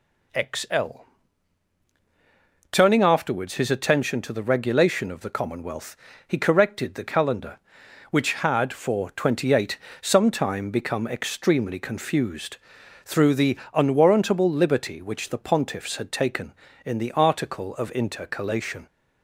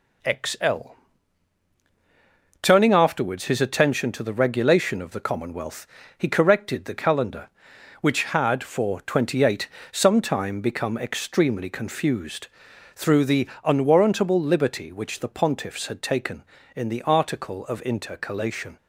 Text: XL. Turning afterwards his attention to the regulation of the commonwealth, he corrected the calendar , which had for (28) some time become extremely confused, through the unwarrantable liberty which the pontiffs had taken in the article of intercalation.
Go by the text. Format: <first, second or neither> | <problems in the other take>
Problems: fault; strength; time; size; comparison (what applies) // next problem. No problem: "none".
first | gets quieter; throughout; 4 dB // pauses between "the" and "unwarrantable"; slight; at 13.4 s; 0.16 s long; slight in the first